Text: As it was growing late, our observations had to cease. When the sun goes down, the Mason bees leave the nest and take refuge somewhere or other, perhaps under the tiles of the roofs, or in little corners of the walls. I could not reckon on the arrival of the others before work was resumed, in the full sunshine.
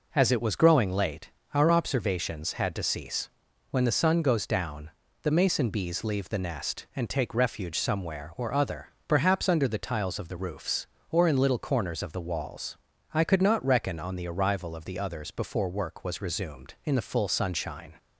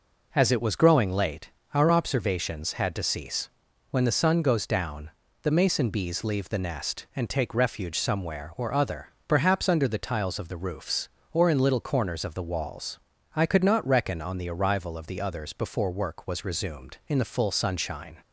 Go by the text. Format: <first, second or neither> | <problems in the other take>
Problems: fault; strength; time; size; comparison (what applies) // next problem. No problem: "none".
neither | none